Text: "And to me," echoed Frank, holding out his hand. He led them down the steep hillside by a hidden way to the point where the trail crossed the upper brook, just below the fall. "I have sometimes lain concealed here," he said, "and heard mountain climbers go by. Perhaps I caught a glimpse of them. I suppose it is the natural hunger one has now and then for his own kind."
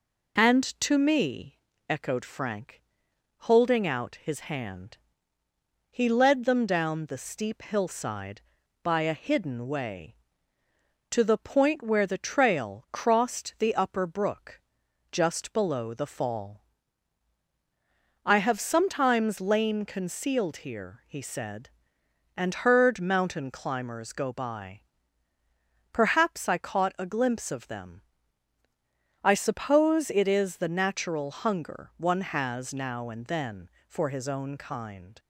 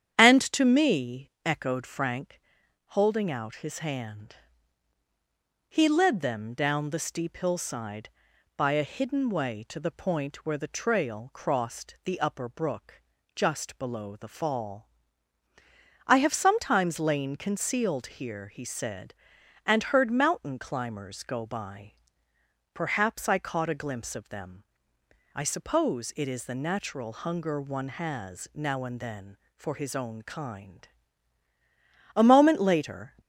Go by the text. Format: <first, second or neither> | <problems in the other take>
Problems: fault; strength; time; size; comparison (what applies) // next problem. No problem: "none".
first | starts louder than the rest; strong; until 1.2 s; 9.5 dB // goes on to say "A moment later"; noticeable; from 32.1 s on; 1.0 s long